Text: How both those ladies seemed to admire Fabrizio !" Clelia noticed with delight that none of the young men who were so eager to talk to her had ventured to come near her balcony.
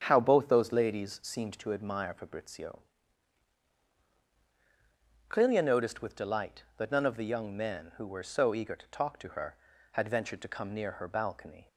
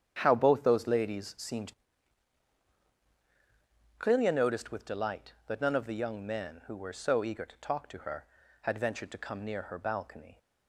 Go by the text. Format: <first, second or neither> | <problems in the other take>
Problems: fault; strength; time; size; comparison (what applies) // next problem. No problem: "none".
first | starts louder than the rest; until 1.2 s; 7 dB; strong in the first // skips "to admire Fabrizio"; at 2.1 s